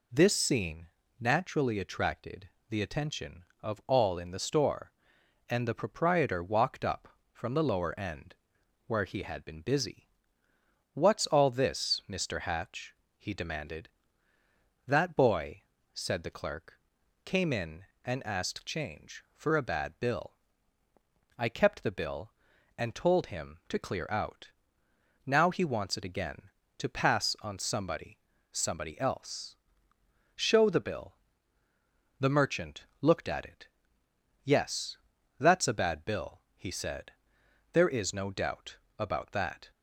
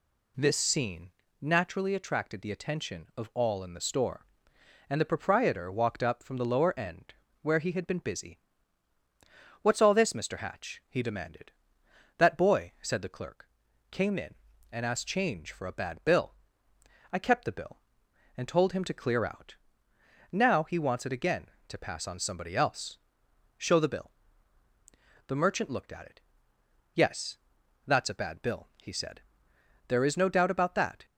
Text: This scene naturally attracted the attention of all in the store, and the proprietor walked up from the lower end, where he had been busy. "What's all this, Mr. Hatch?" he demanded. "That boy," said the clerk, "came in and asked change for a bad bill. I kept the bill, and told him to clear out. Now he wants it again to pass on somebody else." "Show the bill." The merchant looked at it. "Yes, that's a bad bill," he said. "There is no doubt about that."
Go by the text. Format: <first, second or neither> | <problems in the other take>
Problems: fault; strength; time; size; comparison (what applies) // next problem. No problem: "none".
second | pauses between "scene" and "naturally"; slight; at 0.8 s; 0.32 s long; slight in the second // pauses between "attracted" and "the"; slight; at 2.4 s; 0.20 s long // says "somebody" twice; at 28.5 s // pauses between "doubt" and "about"; slight; at 38.7 s; 0.22 s long